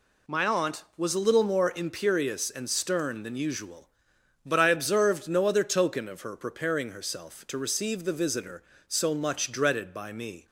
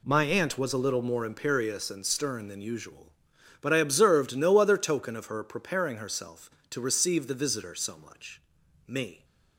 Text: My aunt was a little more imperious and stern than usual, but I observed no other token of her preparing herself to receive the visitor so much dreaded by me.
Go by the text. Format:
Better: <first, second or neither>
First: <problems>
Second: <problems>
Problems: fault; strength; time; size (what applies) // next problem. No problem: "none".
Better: first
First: none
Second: skips "dreaded by"; at 8.6 s